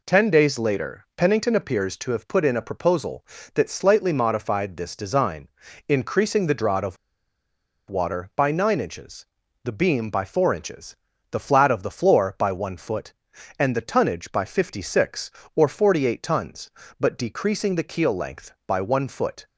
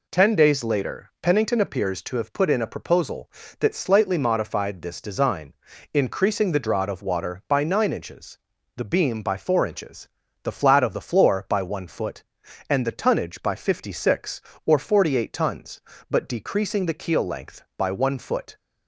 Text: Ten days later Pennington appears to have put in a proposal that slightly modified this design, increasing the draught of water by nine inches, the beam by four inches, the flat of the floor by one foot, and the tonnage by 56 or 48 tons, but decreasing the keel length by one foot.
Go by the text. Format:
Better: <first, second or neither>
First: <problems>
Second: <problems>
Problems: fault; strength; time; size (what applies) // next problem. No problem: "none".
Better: second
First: pauses between "of" and "water"; noticeable; at 6.9 s; 0.92 s long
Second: none